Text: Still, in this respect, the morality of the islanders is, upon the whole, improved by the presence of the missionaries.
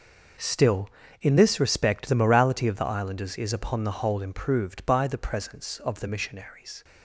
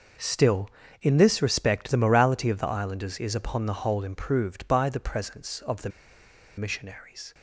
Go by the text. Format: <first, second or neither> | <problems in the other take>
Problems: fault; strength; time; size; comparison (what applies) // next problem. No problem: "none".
first | pauses between "the" and "missionaries"; noticeable; at 5.8 s; 0.67 s long